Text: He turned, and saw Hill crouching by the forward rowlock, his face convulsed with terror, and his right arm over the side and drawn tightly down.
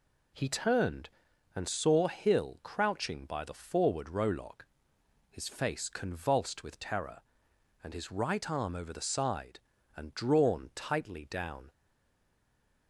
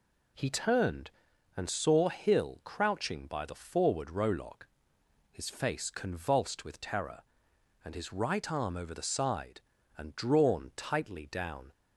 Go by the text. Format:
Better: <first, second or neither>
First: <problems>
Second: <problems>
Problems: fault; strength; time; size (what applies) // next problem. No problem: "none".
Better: second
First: stays silent after the last word; noticeable; from 11.7 s on; 1.1 s long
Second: none